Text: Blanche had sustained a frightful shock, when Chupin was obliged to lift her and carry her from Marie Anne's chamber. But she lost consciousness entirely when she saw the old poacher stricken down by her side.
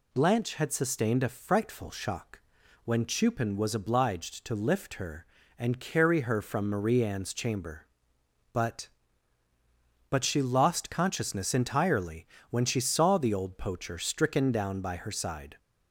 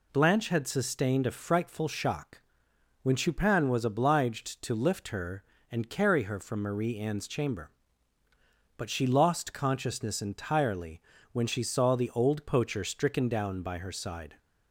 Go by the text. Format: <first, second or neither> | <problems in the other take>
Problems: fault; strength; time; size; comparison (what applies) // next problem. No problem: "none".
second | says "But" twice; at 10.0 s // pauses between "entirely" and "when"; slight; at 12.2 s; 0.24 s long; slight in the second